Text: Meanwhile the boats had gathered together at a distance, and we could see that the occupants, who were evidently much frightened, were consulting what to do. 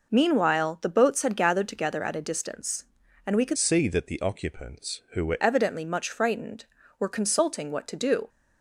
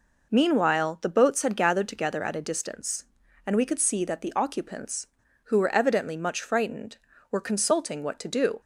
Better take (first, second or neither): second